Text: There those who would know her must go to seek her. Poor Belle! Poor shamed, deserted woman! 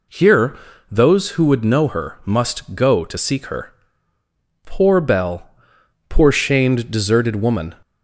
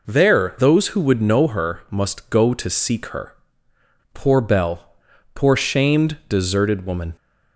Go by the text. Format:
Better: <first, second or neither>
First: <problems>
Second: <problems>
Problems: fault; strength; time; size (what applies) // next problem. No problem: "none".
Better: second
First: says "Here" for "There"; at 0.0 s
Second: none